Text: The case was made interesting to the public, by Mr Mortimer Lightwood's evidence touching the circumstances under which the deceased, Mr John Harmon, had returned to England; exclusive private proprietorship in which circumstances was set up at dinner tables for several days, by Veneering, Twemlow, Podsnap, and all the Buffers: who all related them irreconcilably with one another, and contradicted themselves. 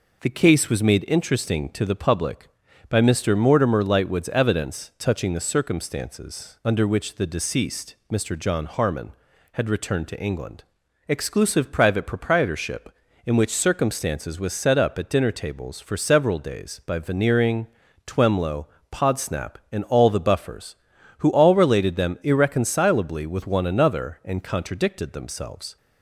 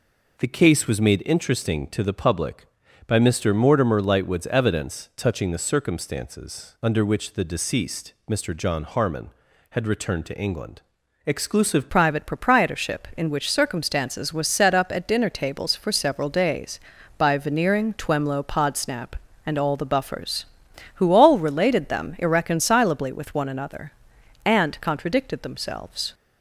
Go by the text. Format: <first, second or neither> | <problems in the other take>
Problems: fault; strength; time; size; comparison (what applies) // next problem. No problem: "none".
first | changes voice at "private"; from 11.8 s on; 14.3 s long